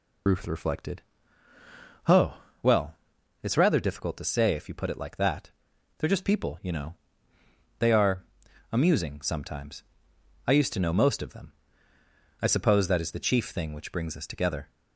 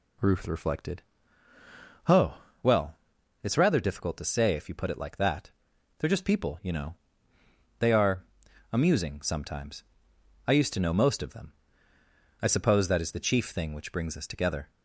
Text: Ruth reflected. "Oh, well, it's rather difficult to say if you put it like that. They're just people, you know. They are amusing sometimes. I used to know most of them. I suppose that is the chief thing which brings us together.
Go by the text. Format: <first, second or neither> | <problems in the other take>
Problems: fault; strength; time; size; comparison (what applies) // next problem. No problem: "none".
second | loses the start of "Ruth"; at 0.2 s; 70 ms // pauses between "are" and "amusing"; noticeable; at 8.2 s; 0.48 s long; noticeable in the second